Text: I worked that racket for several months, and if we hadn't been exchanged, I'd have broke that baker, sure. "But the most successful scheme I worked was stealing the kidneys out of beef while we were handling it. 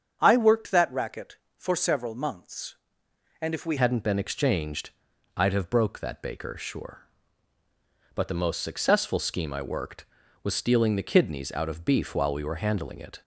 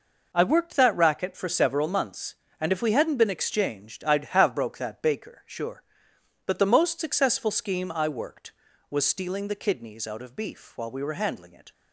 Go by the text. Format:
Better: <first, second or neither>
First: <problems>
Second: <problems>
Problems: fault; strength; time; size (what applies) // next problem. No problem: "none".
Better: second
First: starts louder than the rest; strong; until 1.2 s; 7.5 dB // changes voice at "hadn't"; from 3.7 s on; 9.5 s long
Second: none